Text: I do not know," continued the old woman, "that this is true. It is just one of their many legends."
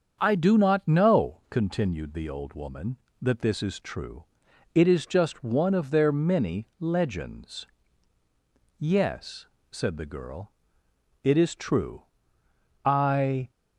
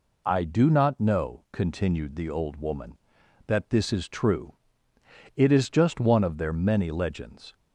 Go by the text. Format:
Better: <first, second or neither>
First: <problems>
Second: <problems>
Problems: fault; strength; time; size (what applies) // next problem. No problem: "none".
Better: second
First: starts louder than the rest; until 1.2 s; 7 dB // goes on to say "Yes said the girl it is true I"; strong; from 8.7 s on; 4.7 s long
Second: none